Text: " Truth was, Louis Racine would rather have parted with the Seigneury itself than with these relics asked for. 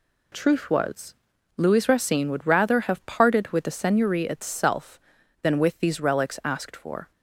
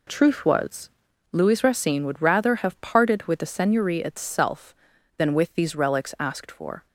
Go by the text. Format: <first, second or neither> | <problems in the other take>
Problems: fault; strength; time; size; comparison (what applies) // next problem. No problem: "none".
first | starts louder than the rest; slight; until 1.2 s; 3 dB